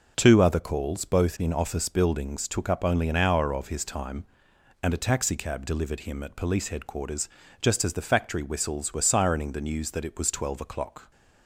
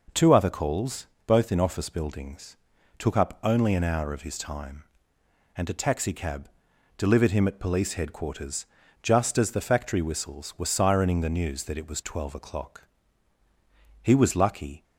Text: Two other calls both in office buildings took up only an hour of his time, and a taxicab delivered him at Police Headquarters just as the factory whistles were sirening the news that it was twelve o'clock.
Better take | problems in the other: first | pauses between "calls" and "both"; slight; at 1.0 s; 0.20 s long // pauses between "buildings" and "took"; at 2.5 s; 0.40 s long // pauses between "taxicab" and "delivered"; noticeable; at 6.4 s; 0.48 s long // pauses between "Headquarters" and "just"; at 8.6 s; 0.38 s long; slight in the first // goes on to say "He was lucky"; noticeable; from 14.0 s on; 0.80 s long

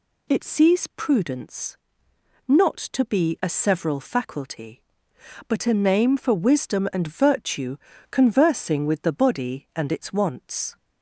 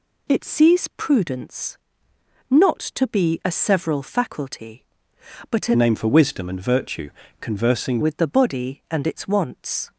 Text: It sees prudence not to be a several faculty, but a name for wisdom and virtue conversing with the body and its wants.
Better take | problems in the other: first | pauses between "prudence" and "not"; noticeable; at 1.7 s; 0.72 s long; noticeable in the first // changes voice from "name" to "conversing"; from 5.7 to 7.9 s; 2.2 s long // pauses between "virtue" and "conversing"; slight; at 7.0 s; 0.30 s long; slight in the first

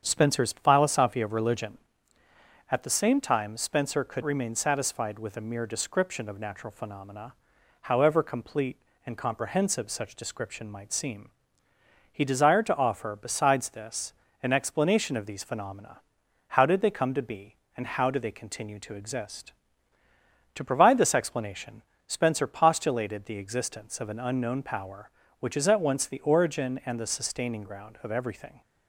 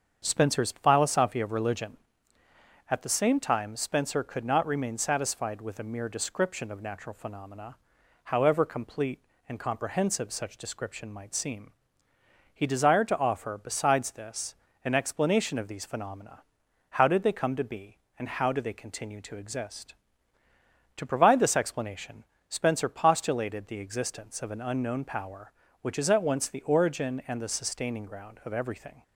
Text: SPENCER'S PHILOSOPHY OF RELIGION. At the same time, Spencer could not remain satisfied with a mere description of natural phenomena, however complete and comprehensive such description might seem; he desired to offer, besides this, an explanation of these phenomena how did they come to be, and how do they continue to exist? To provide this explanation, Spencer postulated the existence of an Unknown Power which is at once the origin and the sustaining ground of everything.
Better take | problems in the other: second | starts louder than the rest; strong; until 1.0 s; 7.5 dB; strong in the second // skips "not"; at 4.2 s // pauses between "phenomena" and "how"; noticeable; at 16.0 s; 0.46 s long; noticeable in the second

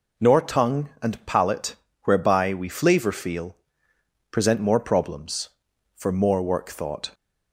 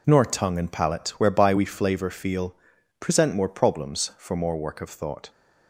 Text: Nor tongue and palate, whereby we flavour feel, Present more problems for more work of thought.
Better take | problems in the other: second | skips "of"; at 6.6 s

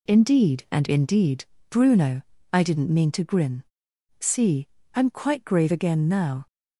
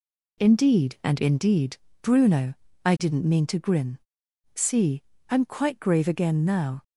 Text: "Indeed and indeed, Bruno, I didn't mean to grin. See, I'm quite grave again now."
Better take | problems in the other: neither | none

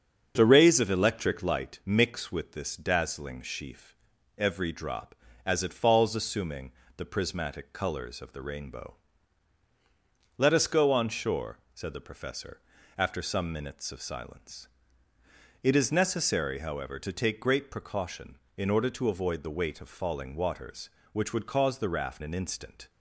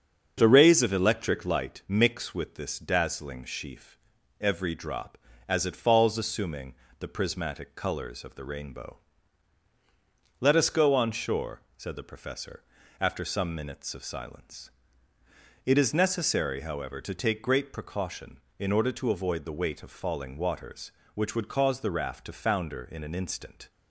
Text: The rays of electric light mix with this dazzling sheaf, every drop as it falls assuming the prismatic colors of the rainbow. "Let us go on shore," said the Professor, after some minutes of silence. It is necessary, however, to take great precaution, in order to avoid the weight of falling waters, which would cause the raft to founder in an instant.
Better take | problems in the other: second | starts louder than the rest; strong; until 1.3 s; 7.5 dB; strong in the second // pauses between "assuming" and "the"; slight; at 6.7 s; 0.26 s long; slight in the second // skips "to founder in"; at 22.2 s

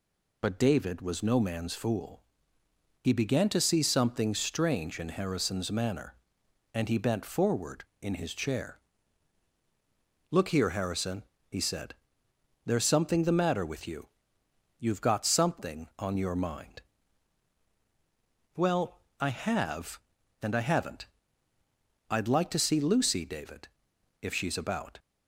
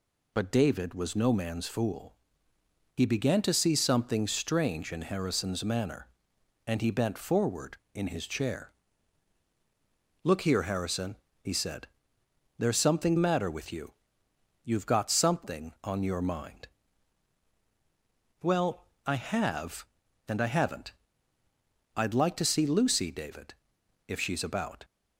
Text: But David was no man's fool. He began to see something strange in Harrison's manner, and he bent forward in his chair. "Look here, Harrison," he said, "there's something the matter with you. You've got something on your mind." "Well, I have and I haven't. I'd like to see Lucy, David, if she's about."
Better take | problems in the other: first | skips "the"; at 13.1 s

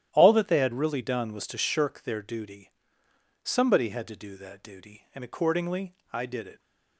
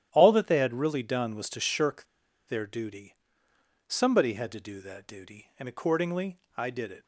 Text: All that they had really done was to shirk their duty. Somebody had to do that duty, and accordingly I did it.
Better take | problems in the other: first | starts louder than the rest; strong; until 1.1 s; 11.5 dB; strong in the first // pauses between "shirk" and "their"; at 2.0 s; 0.42 s long // pauses between "accordingly" and "I"; slight; at 6.3 s; 0.18 s long; slight in the first

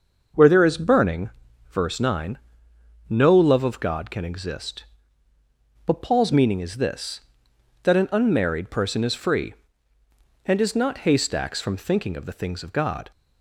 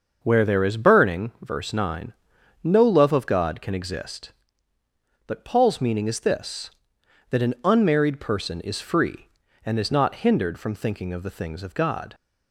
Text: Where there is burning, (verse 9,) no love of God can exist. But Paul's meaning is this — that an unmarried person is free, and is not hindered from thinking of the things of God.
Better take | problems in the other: second | starts louder than the rest; noticeable; until 1.7 s; 6 dB; also in the second // says "haystacks" for "hindered"; at 11.0 s

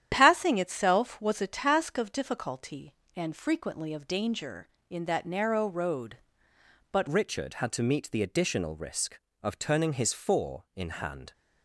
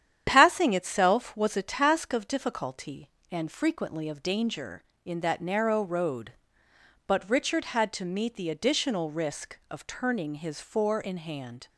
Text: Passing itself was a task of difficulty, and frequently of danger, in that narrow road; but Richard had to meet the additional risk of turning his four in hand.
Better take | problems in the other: second | starts louder than the rest; strong; until 1.1 s; 10 dB; strong in the second // changes voice at "Richard"; from 7.0 s on; 4.3 s long

